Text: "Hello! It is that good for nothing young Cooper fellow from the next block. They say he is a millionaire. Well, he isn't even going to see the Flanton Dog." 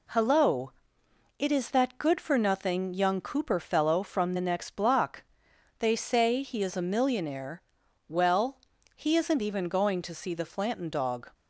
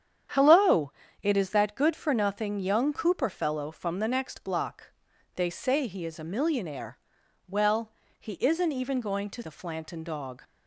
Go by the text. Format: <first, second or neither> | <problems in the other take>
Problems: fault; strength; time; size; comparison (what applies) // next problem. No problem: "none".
first | starts louder than the rest; strong; until 1.6 s; 9 dB // skips "see"; at 9.4 s